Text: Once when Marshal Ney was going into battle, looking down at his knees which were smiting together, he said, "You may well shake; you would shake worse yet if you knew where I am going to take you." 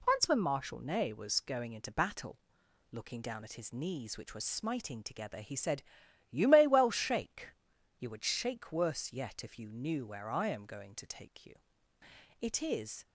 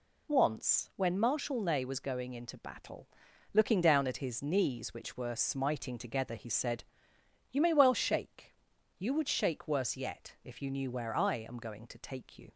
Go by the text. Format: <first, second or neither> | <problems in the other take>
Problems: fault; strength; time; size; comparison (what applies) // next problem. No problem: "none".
second | goes on to say "It is"; noticeable; from 12.3 s on; 0.66 s long